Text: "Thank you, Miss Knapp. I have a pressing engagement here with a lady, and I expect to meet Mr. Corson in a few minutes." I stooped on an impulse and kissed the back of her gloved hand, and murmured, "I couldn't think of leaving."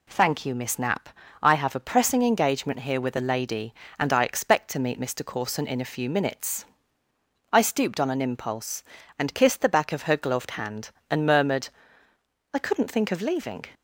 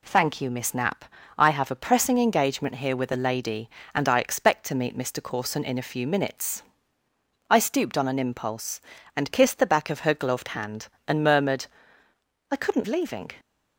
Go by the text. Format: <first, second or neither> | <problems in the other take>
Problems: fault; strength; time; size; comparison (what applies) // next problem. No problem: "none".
first | skips "think of"; at 12.8 s